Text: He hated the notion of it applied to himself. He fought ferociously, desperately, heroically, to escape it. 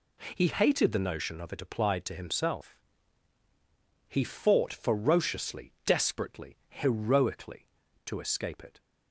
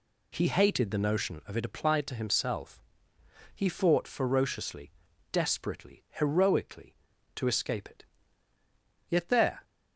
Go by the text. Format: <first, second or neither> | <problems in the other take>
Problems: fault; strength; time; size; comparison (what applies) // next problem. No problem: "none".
first | goes on to say "Yet there"; from 9.1 s on; 0.52 s long